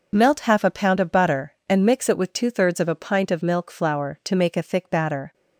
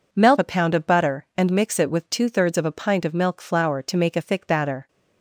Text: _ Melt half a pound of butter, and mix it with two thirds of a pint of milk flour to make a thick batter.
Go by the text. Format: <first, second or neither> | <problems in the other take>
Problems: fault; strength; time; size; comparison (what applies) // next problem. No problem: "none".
first | skips "half"; at 0.3 s